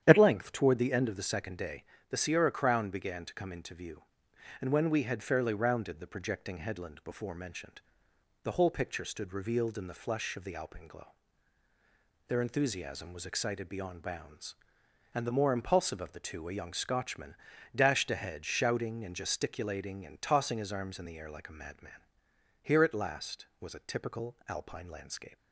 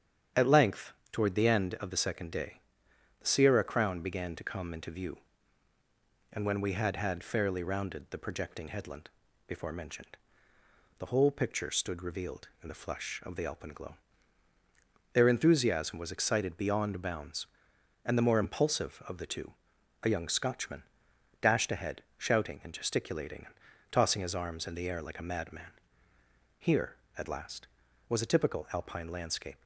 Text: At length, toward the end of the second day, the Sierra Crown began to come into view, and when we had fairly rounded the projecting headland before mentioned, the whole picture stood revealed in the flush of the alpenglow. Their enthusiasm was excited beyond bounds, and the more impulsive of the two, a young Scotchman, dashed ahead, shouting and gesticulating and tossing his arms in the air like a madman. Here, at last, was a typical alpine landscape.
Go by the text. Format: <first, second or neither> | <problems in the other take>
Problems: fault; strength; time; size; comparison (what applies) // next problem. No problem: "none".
first | starts louder than the rest; strong; until 1.5 s; 9 dB; strong in the first // says "had" twice; at 6.9 s // pauses between "headland" and "before"; slight; at 9.0 s; 0.36 s long // pauses between "and" and "tossing"; slight; at 23.5 s; 0.36 s long